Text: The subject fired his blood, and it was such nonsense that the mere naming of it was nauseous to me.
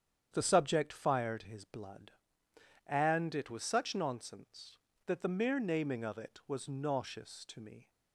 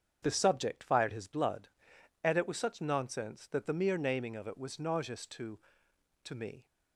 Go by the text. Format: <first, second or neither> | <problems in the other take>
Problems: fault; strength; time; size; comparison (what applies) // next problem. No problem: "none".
first | starts louder than the rest; strong; until 1.2 s; 7.5 dB; strong in the first // says "to" twice; at 6.2 s